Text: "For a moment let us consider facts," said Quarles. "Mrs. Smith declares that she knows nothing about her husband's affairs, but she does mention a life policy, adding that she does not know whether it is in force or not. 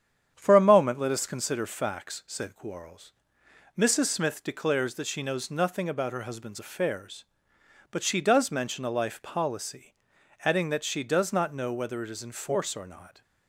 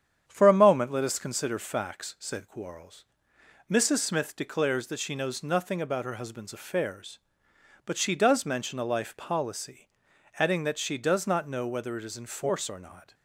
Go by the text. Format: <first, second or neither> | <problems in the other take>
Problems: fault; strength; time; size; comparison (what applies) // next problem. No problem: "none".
neither | starts louder than the rest; strong; the same in both